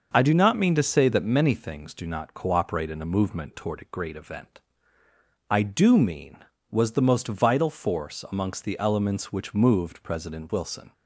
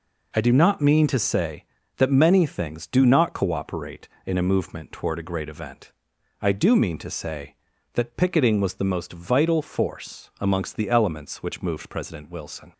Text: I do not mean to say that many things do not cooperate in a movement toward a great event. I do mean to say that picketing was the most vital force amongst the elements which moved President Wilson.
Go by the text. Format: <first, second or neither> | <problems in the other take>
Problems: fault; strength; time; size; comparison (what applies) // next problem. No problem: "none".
second | starts louder than the rest; noticeable; until 1.1 s; 6 dB // skips "to say that picketing"; at 6.5 s